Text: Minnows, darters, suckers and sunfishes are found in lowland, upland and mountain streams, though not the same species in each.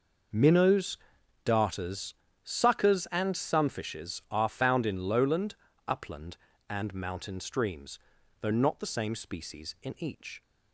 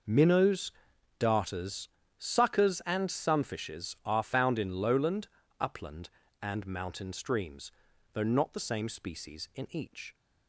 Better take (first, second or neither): neither